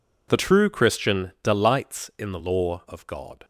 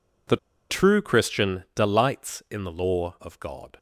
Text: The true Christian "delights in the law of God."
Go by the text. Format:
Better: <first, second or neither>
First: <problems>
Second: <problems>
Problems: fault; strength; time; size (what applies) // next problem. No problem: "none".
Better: first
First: none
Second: pauses between "The" and "true"; slight; at 0.3 s; 0.33 s long